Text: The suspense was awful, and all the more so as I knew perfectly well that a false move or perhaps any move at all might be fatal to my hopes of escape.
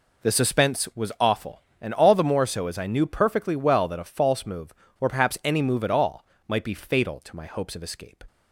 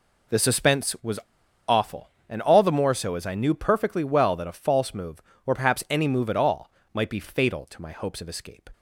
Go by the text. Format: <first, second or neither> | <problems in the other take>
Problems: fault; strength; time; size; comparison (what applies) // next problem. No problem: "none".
first | pauses between "was" and "awful"; noticeable; at 1.1 s; 0.48 s long // pauses between "all" and "might"; slight; at 6.7 s; 0.24 s long; slight in the first